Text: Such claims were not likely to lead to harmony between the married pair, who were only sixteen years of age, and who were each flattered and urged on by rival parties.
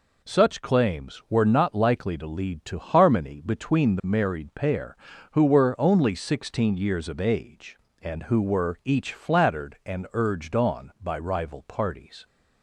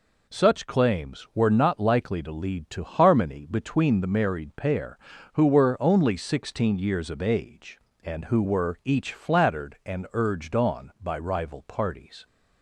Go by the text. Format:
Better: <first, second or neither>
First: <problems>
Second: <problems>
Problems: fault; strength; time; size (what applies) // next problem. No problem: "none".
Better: neither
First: none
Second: none